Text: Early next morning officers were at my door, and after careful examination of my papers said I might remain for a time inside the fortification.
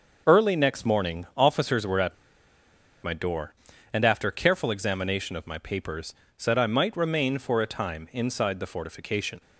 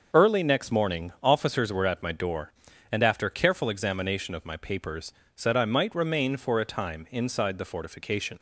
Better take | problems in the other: second | starts louder than the rest; until 1.3 s; 6 dB; also in the second // pauses between "at" and "my"; noticeable; at 2.1 s; 0.86 s long // pauses between "papers" and "said"; slight; at 6.1 s; 0.24 s long; slight in the second

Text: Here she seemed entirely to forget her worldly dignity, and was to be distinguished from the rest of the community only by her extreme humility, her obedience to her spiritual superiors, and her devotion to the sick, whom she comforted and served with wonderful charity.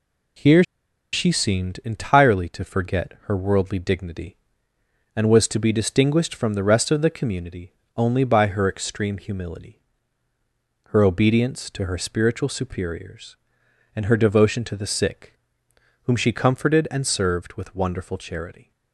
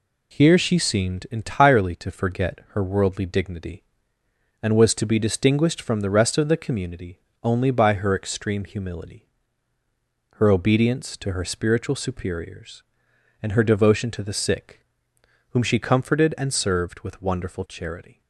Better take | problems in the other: second | pauses between "Here" and "she"; noticeable; at 0.6 s; 0.49 s long // pauses between "community" and "only"; slight; at 7.7 s; 0.24 s long; slight in the second

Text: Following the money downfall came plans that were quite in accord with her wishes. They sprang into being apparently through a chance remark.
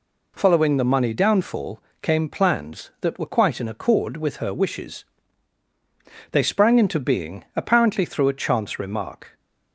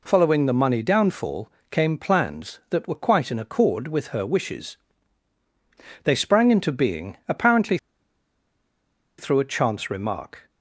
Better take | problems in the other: first | pauses between "downfall" and "came"; slight; at 1.4 s; 0.22 s long; slight in the first // pauses between "apparently" and "through"; strong; at 7.7 s; 1.4 s long

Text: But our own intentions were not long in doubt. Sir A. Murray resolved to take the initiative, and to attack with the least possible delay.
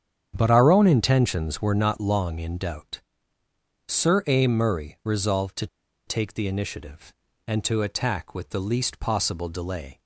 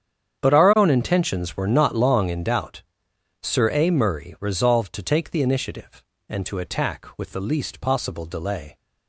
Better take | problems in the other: second | starts louder than the rest; strong; until 1.3 s; 8.5 dB; strong in the second // pauses between "to" and "take"; at 5.6 s; 0.40 s long

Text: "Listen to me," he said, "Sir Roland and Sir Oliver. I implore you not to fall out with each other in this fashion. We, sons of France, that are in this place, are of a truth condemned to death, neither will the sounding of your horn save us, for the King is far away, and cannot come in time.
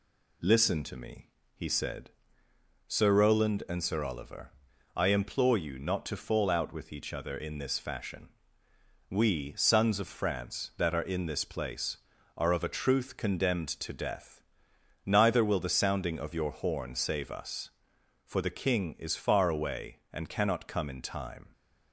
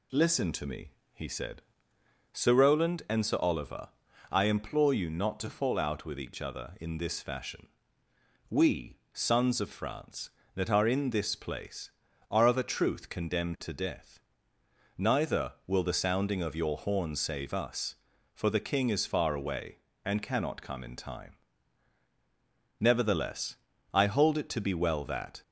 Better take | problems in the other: first | goes on to say "Nevertheless I hold it to be well that"; strong; from 22.7 s on; 2.6 s long

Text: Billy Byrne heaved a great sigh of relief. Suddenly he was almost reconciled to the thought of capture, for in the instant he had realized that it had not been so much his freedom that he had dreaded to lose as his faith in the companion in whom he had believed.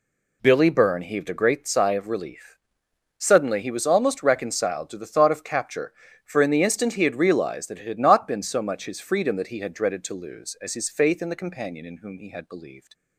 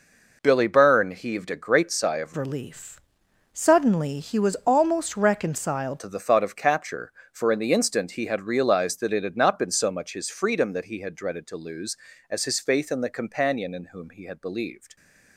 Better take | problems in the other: first | changes voice from "relief" to "reconciled"; from 2.3 to 6.0 s; 3.7 s long

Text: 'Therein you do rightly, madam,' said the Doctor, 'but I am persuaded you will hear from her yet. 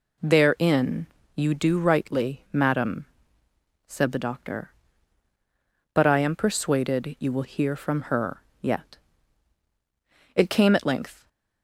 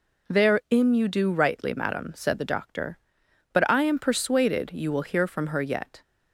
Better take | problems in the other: second | pauses between "Therein" and "you"; slight; at 1.0 s; 0.30 s long // pauses between "her" and "yet"; slight; at 8.4 s; 0.18 s long // goes on to say "It came at length"; noticeable; from 10.3 s on; 0.92 s long

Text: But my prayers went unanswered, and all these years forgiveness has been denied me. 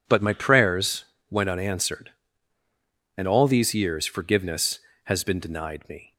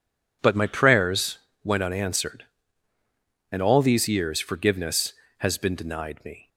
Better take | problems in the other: neither | pauses between "prayers" and "went"; slight; the same in both

